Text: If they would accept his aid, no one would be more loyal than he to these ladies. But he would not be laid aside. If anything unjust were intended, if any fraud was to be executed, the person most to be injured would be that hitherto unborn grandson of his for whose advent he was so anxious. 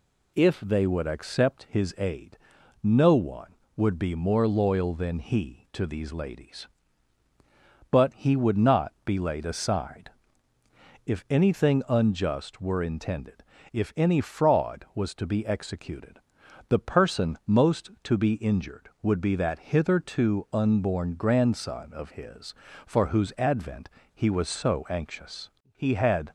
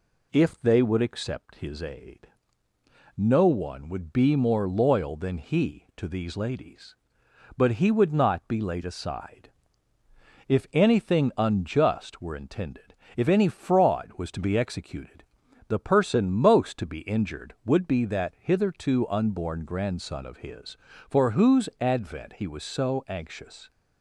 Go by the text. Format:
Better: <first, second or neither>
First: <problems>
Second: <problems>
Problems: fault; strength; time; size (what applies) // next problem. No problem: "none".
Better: second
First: pauses between "advent" and "he"; slight; at 23.8 s; 0.24 s long // goes on to say "He had"; from 25.7 s on; 0.58 s long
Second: none